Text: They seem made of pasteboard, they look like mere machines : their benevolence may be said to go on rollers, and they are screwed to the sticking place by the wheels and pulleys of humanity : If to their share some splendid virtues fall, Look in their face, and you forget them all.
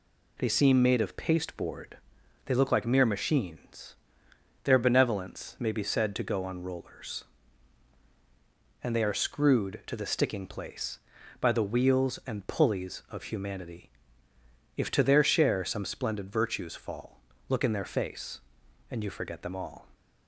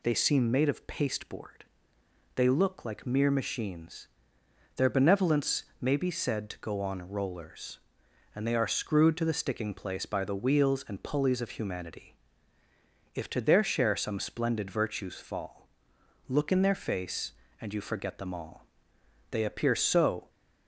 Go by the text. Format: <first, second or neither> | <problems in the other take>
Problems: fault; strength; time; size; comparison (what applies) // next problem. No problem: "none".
first | pauses between "benevolence" and "may"; slight; at 5.6 s; 0.16 s long // goes on to say "They appear so"; noticeable; from 19.2 s on; 1.0 s long